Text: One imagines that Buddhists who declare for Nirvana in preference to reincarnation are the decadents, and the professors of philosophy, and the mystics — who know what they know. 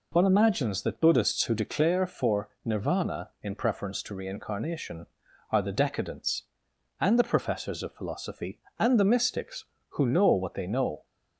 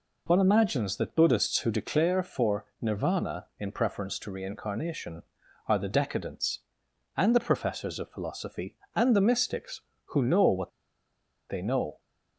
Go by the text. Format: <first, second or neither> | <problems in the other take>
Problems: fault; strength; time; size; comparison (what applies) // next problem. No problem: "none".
first | pauses between "for" and "Nirvana"; slight; at 2.6 s; 0.16 s long; slight in the first // pauses between "what" and "they"; noticeable; at 10.7 s; 0.79 s long